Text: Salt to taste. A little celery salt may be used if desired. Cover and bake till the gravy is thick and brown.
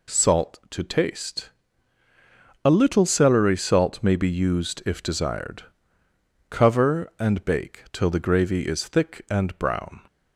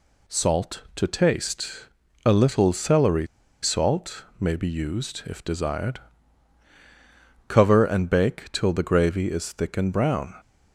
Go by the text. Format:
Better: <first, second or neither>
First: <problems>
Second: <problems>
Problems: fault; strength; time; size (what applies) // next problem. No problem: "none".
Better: first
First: none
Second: pauses between "celery" and "salt"; slight; at 3.2 s; 0.35 s long